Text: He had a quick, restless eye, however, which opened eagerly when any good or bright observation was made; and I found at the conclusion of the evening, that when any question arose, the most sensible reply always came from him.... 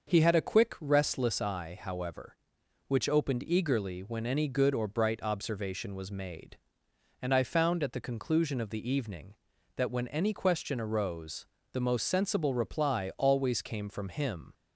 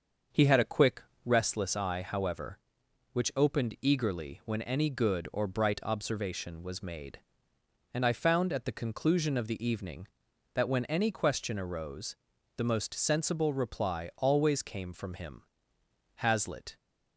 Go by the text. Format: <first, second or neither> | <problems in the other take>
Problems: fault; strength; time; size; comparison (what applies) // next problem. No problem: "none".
first | starts louder than the rest; until 1.5 s; 6.5 dB; also in the first // goes on to say "Hazlitt"; from 16.1 s on; 0.60 s long